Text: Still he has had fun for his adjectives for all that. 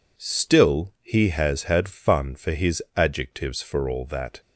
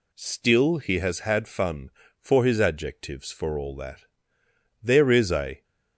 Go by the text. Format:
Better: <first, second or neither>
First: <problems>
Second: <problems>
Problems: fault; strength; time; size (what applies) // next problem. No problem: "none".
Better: first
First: none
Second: goes on to say "There is a"; noticeable; from 4.8 s on; 0.80 s long